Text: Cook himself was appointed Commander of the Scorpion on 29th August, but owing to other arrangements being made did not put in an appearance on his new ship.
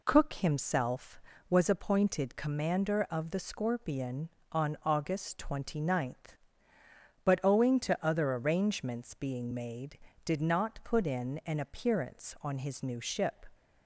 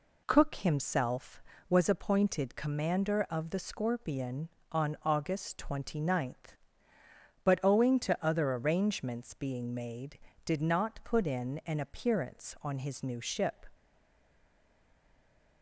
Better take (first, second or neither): first